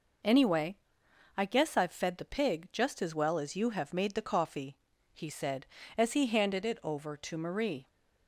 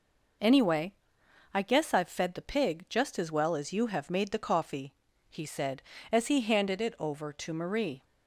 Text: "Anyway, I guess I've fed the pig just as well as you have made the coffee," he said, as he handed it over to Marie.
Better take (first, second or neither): neither